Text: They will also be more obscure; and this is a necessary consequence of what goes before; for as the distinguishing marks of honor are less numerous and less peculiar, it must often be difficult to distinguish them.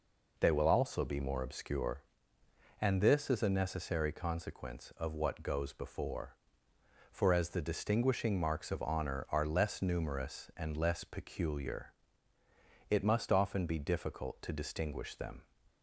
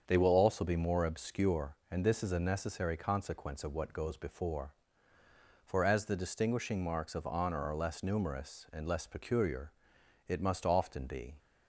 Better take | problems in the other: first | starts louder than the rest; strong; until 1.0 s; 7 dB // stops before "difficult to distinguish them"; at 11.3 s

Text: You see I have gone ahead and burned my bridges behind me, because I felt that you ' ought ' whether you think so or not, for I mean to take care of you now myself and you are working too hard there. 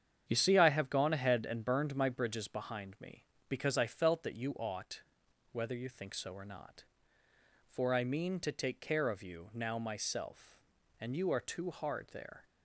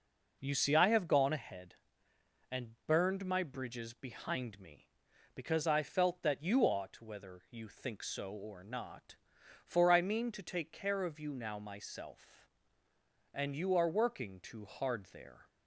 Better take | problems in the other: second | starts louder than the rest; strong; until 1.2 s; 8.5 dB // skips "working"; at 11.3 s

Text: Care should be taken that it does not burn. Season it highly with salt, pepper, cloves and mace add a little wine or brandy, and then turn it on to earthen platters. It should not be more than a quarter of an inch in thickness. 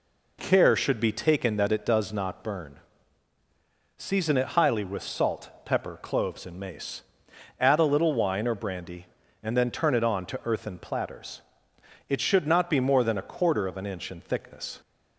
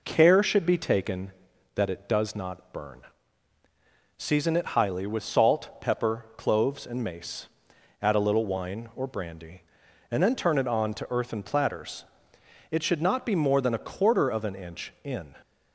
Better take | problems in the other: first | pauses between "mace" and "add"; noticeable; at 7.4 s; 0.54 s long; noticeable in the first // stops before "thickness"; at 15.4 s

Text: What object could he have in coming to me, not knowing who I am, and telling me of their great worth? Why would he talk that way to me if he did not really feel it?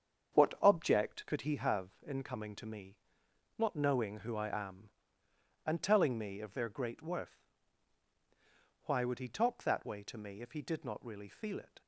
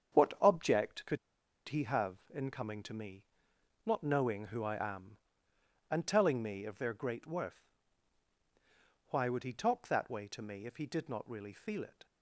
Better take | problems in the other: first | starts louder than the rest; strong; until 1.7 s; 7.5 dB; strong in the first // pauses between "could" and "he"; noticeable; at 1.1 s; 0.51 s long

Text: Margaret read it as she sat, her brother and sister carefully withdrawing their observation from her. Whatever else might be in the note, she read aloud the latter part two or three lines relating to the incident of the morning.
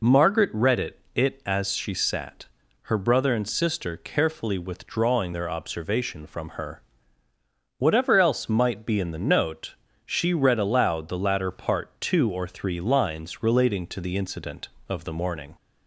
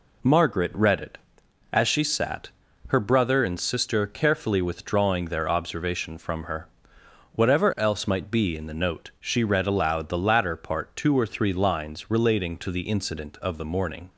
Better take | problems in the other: second | says "it" twice; at 1.1 s

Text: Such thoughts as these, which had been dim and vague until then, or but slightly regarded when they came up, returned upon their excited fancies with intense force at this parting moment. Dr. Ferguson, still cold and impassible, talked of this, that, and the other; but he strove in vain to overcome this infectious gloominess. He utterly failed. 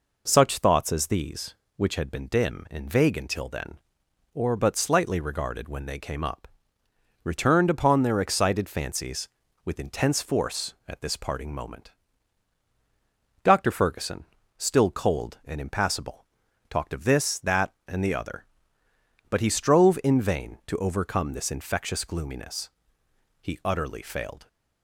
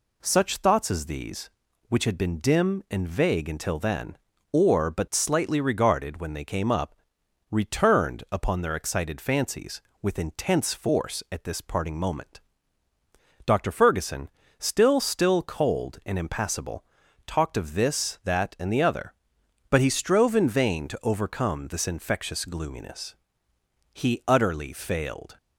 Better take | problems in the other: first | says "still" twice; at 14.9 s

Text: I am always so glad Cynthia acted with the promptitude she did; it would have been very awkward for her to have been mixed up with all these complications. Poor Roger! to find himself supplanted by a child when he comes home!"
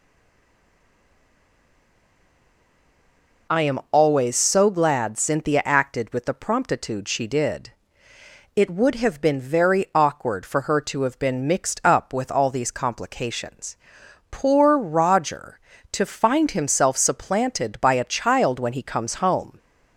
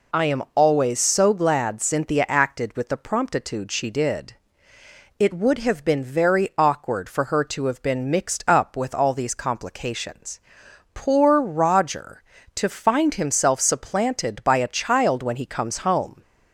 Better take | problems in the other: second | stays silent before the first word; strong; until 3.4 s; 3.4 s long

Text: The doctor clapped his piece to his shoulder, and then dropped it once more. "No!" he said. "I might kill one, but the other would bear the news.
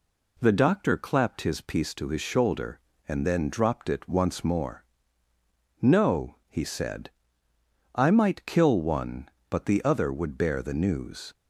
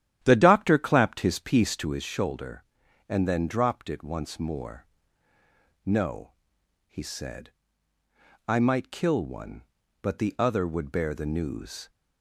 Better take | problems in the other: first | starts louder than the rest; strong; until 2.0 s; 11.5 dB

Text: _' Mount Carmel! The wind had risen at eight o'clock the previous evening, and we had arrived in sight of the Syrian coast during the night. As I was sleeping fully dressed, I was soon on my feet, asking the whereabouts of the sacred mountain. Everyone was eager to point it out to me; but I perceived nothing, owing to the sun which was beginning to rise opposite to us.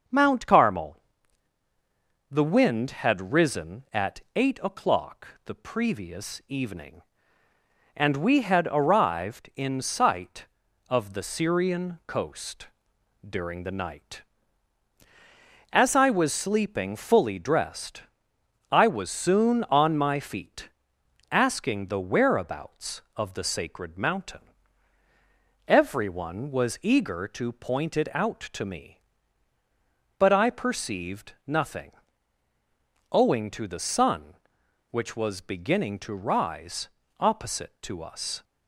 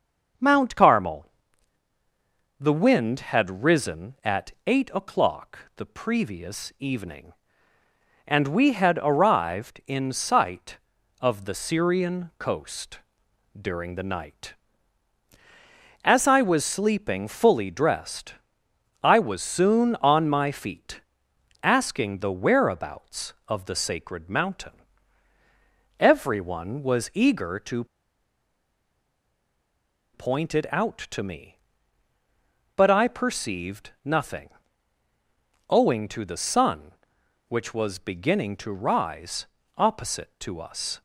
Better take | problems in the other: first | starts louder than the rest; noticeable; until 2.7 s; 6 dB; noticeable in the first // pauses between "at" and "eight"; slight; at 4.5 s; 0.16 s long; slight in the first // pauses between "o'clock" and "the"; slight; at 5.5 s; 0.18 s long; slight in the first // pauses between "coast" and "during"; noticeable; at 12.9 s; 0.60 s long; noticeable in the first // pauses between "to" and "point"; strong; at 27.8 s; 2.2 s long // pauses between "rise" and "opposite"; slight; at 39.4 s; 0.32 s long; slight in the first

